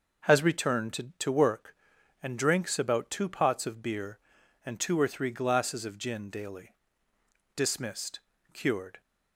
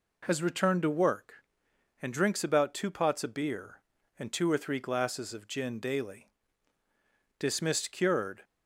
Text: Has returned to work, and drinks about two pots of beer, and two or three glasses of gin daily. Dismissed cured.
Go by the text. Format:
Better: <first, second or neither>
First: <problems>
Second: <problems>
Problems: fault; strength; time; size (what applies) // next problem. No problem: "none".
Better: second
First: says "to" twice; at 1.1 s // pauses between "Dismissed" and "cured"; slight; at 8.2 s; 0.32 s long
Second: none